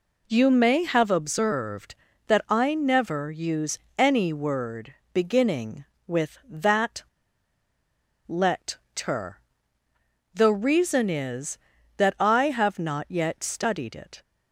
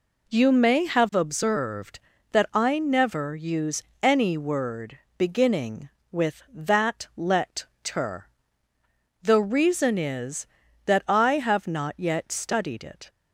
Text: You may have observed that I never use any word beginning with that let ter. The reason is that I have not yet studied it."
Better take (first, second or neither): second